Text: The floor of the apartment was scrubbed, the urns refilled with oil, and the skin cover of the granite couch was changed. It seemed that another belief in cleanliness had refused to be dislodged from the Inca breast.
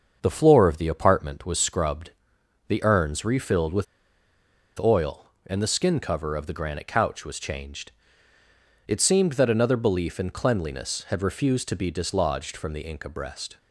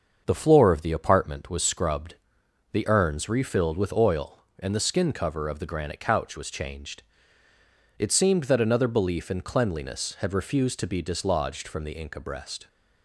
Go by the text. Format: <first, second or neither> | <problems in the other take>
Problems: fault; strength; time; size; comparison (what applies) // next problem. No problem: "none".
second | starts louder than the rest; until 1.2 s; 6.5 dB; also in the second // pauses between "with" and "oil"; noticeable; at 3.8 s; 0.94 s long